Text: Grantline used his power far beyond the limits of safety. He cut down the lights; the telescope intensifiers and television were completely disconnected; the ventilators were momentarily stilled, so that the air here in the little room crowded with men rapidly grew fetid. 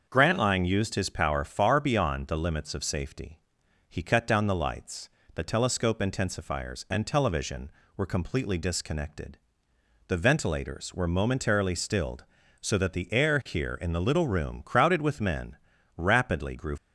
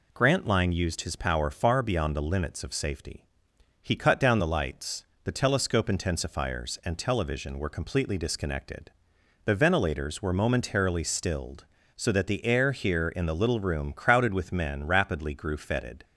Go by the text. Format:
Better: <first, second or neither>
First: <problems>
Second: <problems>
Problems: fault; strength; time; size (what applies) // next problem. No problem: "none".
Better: second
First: starts louder than the rest; until 1.1 s; 6.5 dB // pauses between "men" and "rapidly"; at 15.5 s; 0.40 s long // stops before "fetid"; at 16.7 s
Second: none